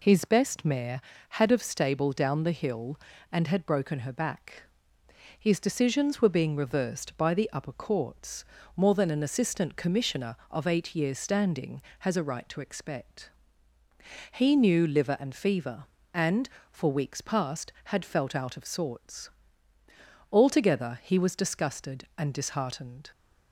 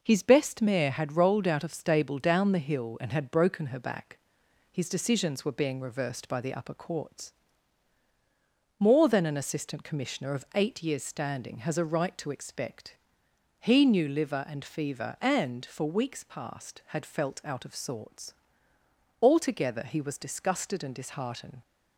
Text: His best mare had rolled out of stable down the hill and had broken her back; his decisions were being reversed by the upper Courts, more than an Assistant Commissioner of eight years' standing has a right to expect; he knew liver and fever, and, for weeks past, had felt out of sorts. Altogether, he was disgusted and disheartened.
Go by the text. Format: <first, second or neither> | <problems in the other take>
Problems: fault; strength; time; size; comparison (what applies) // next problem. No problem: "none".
second | skips "rolled out"; at 1.5 s